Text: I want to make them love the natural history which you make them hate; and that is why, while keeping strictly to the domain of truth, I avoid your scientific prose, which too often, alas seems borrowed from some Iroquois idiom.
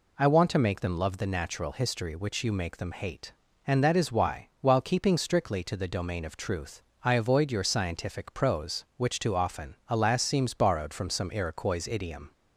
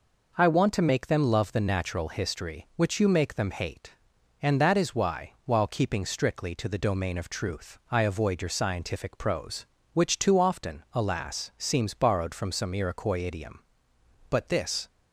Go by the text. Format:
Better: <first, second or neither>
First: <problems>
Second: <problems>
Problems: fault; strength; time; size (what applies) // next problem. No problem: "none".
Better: first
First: none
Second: goes on to say "But this"; from 14.2 s on; 0.58 s long